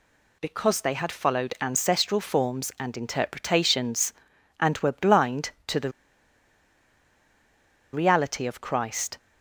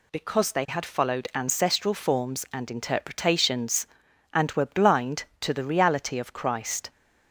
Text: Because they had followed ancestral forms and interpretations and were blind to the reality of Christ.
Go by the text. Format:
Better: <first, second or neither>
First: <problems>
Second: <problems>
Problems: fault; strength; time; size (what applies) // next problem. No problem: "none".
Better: second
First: pauses between "the" and "reality"; strong; at 5.9 s; 2.0 s long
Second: none